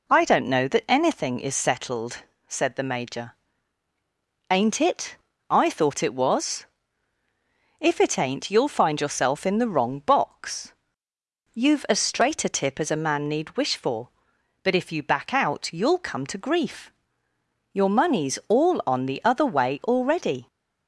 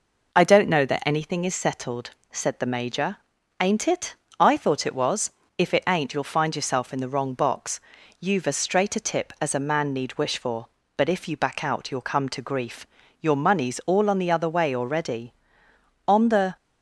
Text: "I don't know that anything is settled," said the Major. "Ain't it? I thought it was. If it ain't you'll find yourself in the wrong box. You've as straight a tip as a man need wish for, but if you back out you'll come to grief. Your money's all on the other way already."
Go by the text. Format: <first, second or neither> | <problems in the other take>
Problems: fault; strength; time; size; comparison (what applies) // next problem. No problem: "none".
first | goes on to say "On the"; slight; from 16.0 s on; 0.48 s long